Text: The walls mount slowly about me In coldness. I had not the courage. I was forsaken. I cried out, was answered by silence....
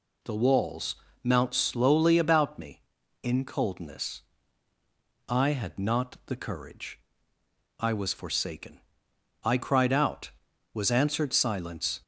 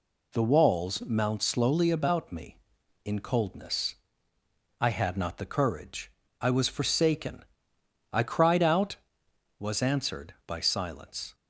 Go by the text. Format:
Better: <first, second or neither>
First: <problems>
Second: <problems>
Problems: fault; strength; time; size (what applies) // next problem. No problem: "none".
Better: second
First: pauses between "walls" and "mount"; slight; at 0.9 s; 0.28 s long // skips "by"; at 11.3 s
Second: none